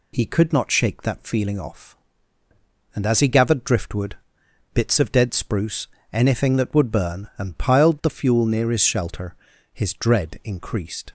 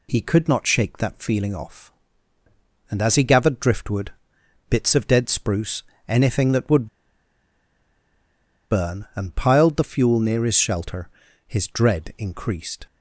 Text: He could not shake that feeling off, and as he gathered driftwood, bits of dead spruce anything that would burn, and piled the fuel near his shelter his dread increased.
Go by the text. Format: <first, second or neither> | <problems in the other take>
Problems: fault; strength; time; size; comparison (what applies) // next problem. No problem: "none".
first | pauses between "spruce" and "anything"; slight; at 5.8 s; 0.24 s long; slight in the first // pauses between "would" and "burn"; strong; at 6.8 s; 1.8 s long // pauses between "shelter" and "his"; slight; at 11.0 s; 0.36 s long; slight in the first